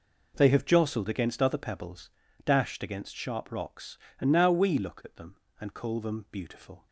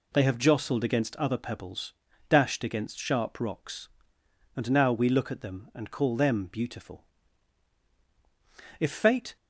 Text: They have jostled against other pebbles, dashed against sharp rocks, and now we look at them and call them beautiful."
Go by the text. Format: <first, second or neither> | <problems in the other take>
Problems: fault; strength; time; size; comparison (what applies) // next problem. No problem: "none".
first | goes on to say "If Fate"; from 8.7 s on; 0.56 s long